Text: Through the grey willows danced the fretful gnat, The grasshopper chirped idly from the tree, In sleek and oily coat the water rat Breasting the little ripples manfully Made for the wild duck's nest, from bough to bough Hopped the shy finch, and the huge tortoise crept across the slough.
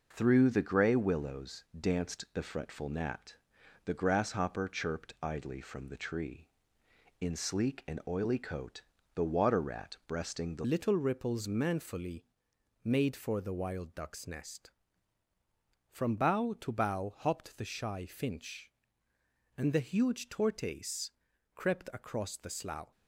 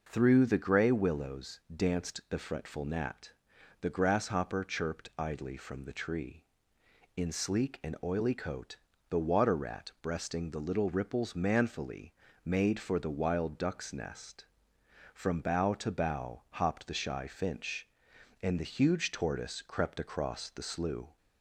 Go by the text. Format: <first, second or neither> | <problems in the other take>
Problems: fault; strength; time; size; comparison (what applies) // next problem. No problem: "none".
second | pauses between "coat" and "the"; slight; at 8.8 s; 0.34 s long; slight in the second // changes voice at "little"; from 10.6 s on; 12.3 s long // pauses between "manfully" and "Made"; noticeable; at 12.2 s; 0.60 s long; slight in the second // pauses between "tortoise" and "crept"; at 21.1 s; 0.42 s long